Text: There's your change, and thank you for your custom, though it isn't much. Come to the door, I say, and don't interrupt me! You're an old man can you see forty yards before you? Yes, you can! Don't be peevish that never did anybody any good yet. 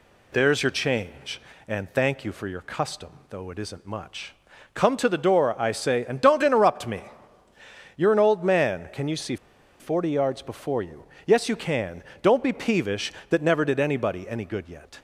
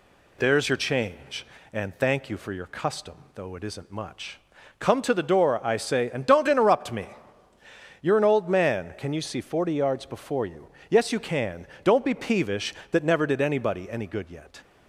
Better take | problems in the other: second | pauses between "see" and "forty"; at 9.3 s; 0.44 s long

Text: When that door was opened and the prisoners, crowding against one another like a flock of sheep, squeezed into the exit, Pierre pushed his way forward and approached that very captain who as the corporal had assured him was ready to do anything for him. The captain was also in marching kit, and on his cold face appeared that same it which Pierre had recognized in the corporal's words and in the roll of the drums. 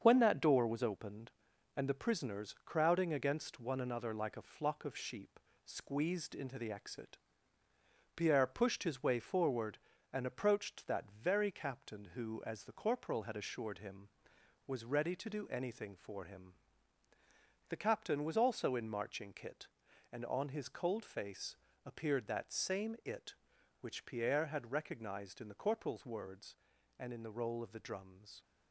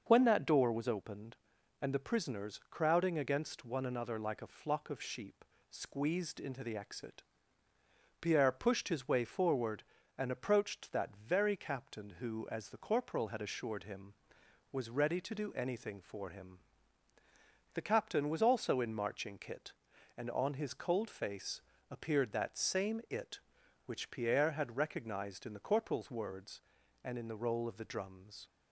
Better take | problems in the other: second | gets quieter; noticeable; throughout; 5.5 dB // starts louder than the rest; strong; until 1.0 s; 7 dB; also in the second // pauses between "face" and "appeared"; slight; at 21.5 s; 0.30 s long; slight in the second

